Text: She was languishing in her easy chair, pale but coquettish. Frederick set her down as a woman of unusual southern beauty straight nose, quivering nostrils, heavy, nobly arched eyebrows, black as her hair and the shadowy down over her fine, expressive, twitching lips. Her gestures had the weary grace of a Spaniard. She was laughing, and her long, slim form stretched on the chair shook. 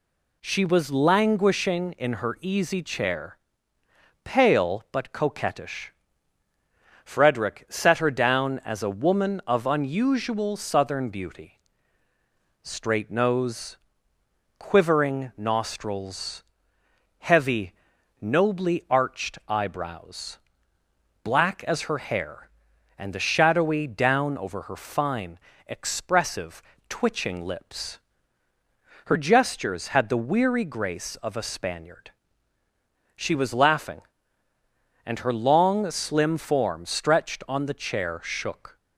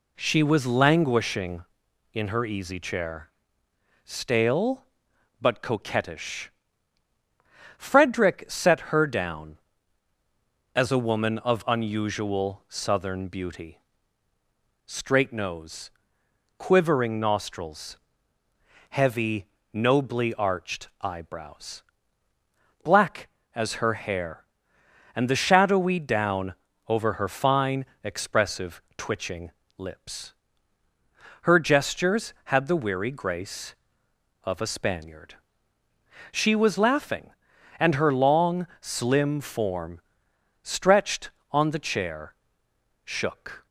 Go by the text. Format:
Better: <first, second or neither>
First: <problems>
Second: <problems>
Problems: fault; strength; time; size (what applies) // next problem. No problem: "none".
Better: first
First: pauses between "beauty" and "straight"; at 11.5 s; 1.0 s long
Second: says "stale" for "pale"; at 4.0 s // pauses between "beauty" and "straight"; at 13.7 s; 1.1 s long // pauses between "down" and "over"; slight; at 26.5 s; 0.34 s long // pauses between "twitching" and "lips"; slight; at 29.5 s; 0.26 s long // pauses between "form" and "stretched"; noticeable; at 40.0 s; 0.62 s long // pauses between "chair" and "shook"; noticeable; at 42.3 s; 0.70 s long